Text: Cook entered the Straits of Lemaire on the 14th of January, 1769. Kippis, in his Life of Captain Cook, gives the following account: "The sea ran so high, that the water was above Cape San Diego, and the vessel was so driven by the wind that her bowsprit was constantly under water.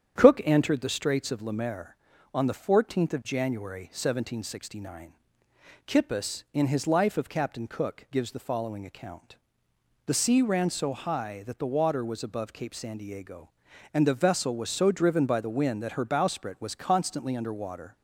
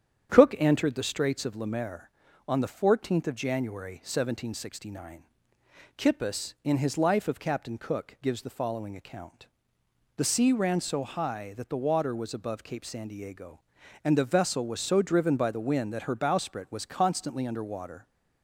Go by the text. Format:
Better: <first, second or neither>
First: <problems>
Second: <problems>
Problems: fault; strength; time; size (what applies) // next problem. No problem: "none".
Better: neither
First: starts louder than the rest; strong; until 1.2 s; 8.5 dB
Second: starts louder than the rest; strong; until 1.3 s; 8.5 dB